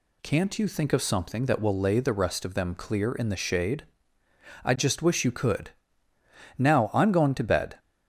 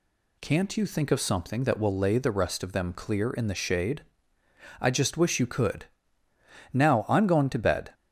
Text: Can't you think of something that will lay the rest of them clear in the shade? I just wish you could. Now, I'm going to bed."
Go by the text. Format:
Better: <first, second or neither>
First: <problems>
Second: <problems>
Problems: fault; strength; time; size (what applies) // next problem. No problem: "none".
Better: neither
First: none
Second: none